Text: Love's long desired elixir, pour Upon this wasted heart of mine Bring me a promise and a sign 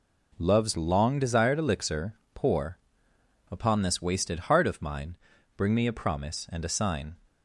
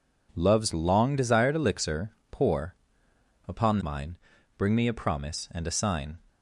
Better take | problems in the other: first | pauses between "pour" and "Upon"; noticeable; at 2.7 s; 0.72 s long; noticeable in the first // skips "this wasted heart of"; at 3.8 s // pauses between "mine" and "Bring"; at 4.1 s; 0.42 s long; also in the first

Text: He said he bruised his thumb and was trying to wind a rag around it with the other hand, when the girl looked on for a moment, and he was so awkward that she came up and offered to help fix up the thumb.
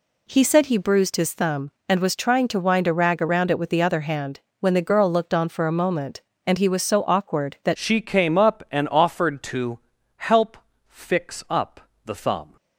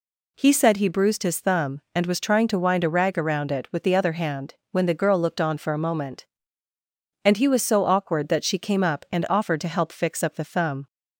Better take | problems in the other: second | changes voice at "she"; from 7.7 s on; 4.8 s long // pauses between "to" and "help"; at 9.7 s; 0.38 s long // pauses between "help" and "fix"; slight; at 10.5 s; 0.32 s long // pauses between "up" and "the"; slight; at 11.8 s; 0.24 s long

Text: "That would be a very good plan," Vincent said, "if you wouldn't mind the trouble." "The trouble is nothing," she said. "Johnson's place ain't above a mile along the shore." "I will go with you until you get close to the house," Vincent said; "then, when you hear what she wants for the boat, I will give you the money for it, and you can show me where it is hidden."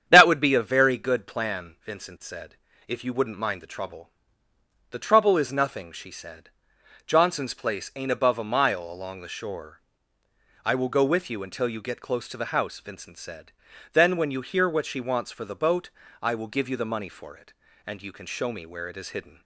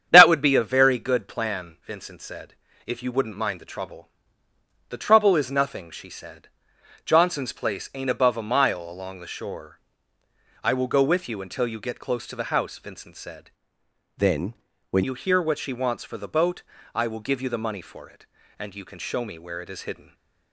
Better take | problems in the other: first | starts louder than the rest; strong; until 1.1 s; 8.5 dB; strong in the first // changes voice from "then" to "when"; from 14.1 to 15.0 s; 0.9 s long // stays silent after the last word; slight; from 20.0 s on; 0.5 s long

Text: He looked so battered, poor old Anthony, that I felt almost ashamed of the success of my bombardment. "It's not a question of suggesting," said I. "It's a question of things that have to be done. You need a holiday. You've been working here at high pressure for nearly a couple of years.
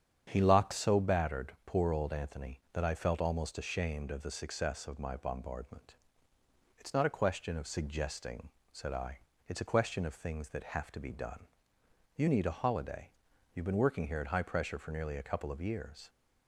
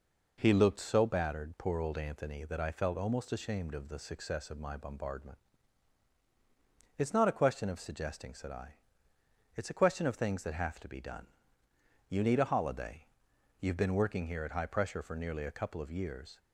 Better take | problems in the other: second | starts louder than the rest; strong; until 1.3 s; 8.5 dB // says "locked" for "looked"; at 0.4 s

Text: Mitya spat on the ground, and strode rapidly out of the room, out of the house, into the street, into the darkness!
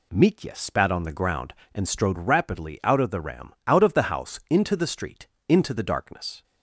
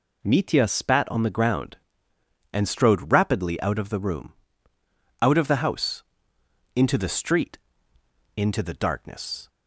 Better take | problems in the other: second | says "ram" for "room"; at 3.2 s

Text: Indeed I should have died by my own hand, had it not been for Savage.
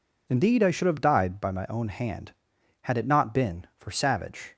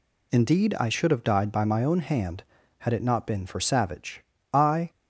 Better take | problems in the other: first | goes on to say "I"; slight; from 4.5 s on; 0.38 s long

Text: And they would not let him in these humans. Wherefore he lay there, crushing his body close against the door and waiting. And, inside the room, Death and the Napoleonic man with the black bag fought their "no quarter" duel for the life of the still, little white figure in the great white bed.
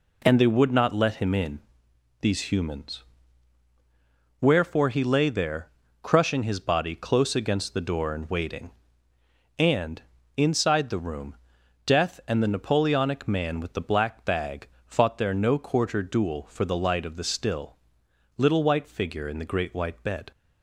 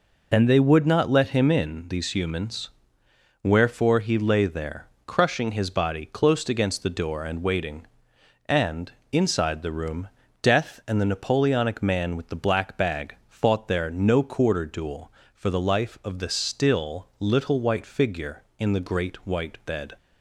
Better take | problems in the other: second | pauses between "in" and "these"; noticeable; at 1.5 s; 0.62 s long // pauses between "bag" and "fought"; slight; at 14.6 s; 0.18 s long // says "light" for "life"; at 16.7 s

